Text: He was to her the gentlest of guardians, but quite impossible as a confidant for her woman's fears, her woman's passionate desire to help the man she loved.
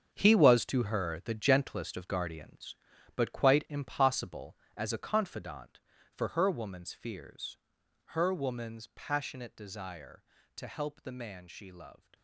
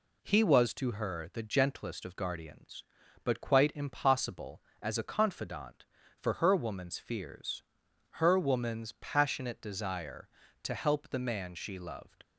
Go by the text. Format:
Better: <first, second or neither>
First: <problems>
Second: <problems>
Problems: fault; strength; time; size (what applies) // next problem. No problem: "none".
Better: second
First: gets quieter; strong; throughout; 12 dB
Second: none